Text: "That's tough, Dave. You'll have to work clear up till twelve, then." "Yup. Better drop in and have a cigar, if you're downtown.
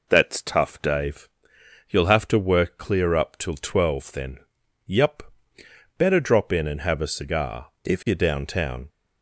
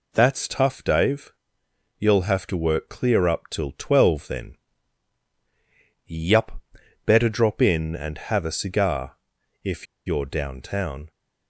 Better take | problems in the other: first | pauses between "if" and "you're"; slight; at 9.8 s; 0.20 s long

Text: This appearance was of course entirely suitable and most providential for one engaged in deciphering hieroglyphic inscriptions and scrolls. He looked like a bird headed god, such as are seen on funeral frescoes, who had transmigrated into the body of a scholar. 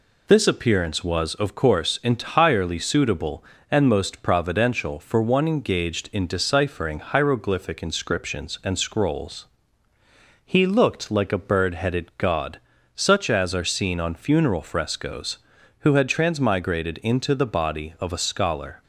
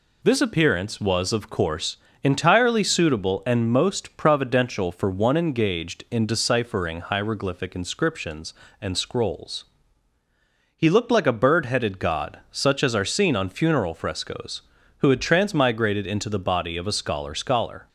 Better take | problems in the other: first | pauses between "course" and "entirely"; slight; at 1.9 s; 0.26 s long // says "scholar" twice; at 17.3 s

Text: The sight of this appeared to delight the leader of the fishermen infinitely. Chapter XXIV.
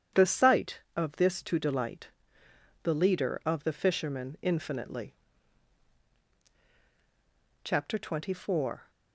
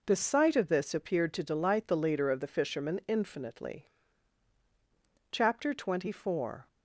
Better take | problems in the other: second | starts louder than the rest; strong; until 1.2 s; 9 dB // skips "appeared"; at 1.4 s // pauses between "delight" and "the"; noticeable; at 2.0 s; 0.74 s long

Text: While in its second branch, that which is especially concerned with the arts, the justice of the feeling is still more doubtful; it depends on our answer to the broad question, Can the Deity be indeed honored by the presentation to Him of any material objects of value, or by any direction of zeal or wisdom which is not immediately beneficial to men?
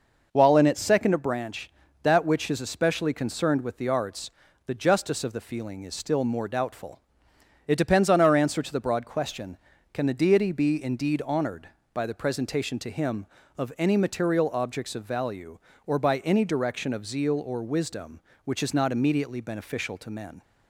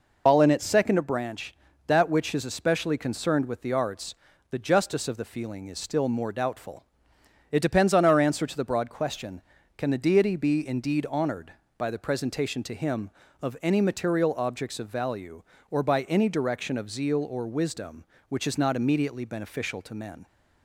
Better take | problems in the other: first | loses the start of "While"; at 0.2 s; 95 ms

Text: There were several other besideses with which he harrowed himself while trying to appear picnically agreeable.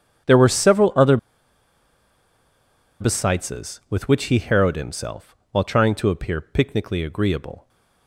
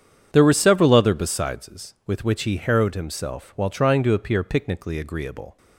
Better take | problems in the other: second | starts louder than the rest; strong; until 3.1 s; 8 dB; strong in the second // pauses between "other" and "besideses"; strong; at 1.1 s; 1.8 s long // pauses between "himself" and "while"; slight; at 5.3 s; 0.16 s long

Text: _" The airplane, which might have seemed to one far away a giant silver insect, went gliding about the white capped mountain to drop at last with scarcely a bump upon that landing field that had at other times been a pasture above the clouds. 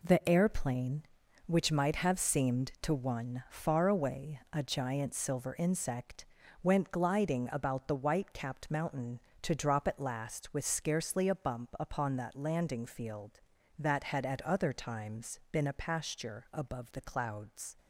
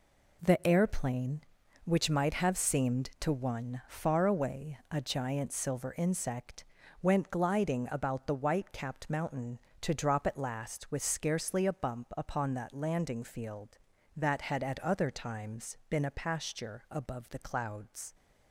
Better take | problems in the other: neither | none

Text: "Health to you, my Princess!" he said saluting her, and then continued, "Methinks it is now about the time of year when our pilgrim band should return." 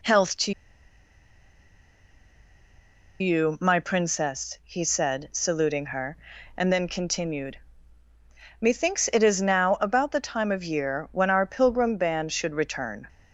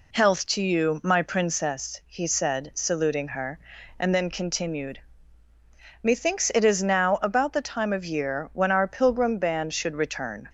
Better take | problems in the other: second | pauses between "to" and "you"; strong; at 0.5 s; 2.6 s long

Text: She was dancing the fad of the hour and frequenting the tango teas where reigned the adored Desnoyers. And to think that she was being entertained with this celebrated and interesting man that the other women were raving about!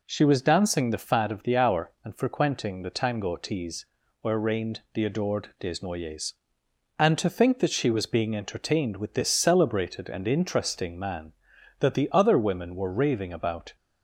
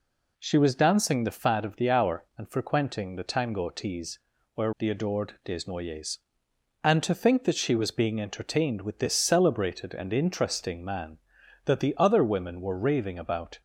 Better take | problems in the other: first | pauses between "teas" and "where"; slight; at 4.1 s; 0.36 s long; slight in the first // skips "reigned"; at 4.7 s

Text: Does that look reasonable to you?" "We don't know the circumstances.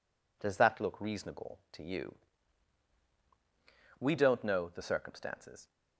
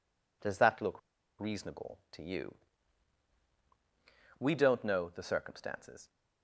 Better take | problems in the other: first | pauses between "look" and "reasonable"; at 0.9 s; 0.39 s long

